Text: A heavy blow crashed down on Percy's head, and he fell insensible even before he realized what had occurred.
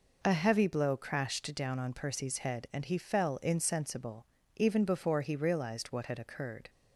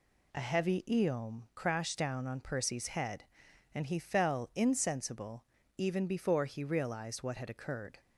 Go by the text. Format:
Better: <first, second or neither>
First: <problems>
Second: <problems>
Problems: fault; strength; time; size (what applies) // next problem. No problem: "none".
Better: first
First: pauses between "insensible" and "even"; slight; at 4.2 s; 0.28 s long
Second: says "eom" for "blow"; at 0.8 s // pauses between "insensible" and "even"; slight; at 5.4 s; 0.34 s long